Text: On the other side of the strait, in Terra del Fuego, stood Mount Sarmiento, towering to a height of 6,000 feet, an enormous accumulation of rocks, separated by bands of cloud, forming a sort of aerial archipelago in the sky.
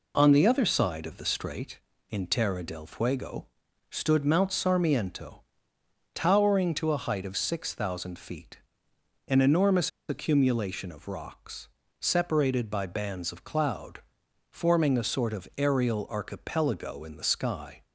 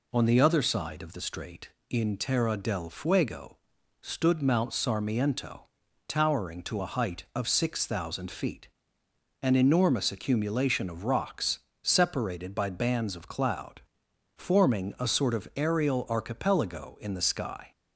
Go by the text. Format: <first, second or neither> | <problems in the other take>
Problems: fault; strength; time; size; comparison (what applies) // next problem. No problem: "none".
second | pauses between "enormous" and "accumulation"; slight; at 9.8 s; 0.18 s long